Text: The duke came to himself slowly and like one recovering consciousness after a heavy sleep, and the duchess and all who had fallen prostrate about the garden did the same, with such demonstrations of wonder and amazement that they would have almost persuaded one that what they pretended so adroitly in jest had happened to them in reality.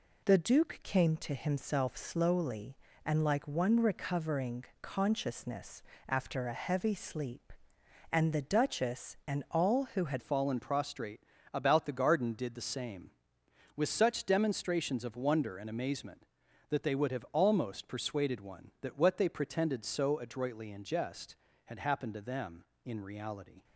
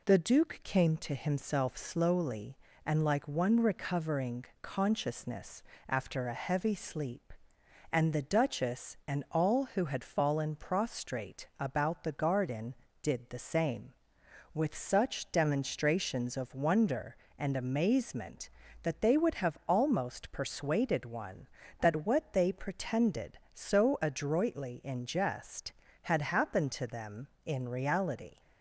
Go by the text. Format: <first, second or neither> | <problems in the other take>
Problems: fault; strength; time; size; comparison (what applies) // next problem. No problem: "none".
second | pauses between "recovering" and "consciousness"; slight; at 4.6 s; 0.18 s long; slight in the second // pauses between "consciousness" and "after"; slight; at 5.8 s; 0.26 s long; slight in the second // changes voice at "fallen"; from 10.2 s on; 13.4 s long // pauses between "prostrate" and "about"; slight; at 11.2 s; 0.32 s long